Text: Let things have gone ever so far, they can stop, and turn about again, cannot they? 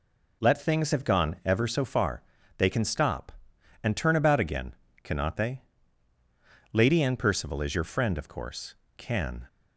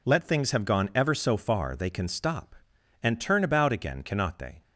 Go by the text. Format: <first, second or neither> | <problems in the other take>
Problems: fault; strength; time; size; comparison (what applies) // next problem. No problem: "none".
second | goes on to say "Lady Anne Percival is your friend of course can"; strong; from 6.7 s on; 2.7 s long